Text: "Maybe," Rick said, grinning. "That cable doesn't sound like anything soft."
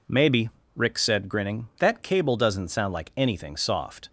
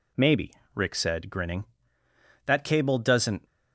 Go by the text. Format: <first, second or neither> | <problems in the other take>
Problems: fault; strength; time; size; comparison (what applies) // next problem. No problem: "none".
first | stops before "sound like anything soft"; at 3.4 s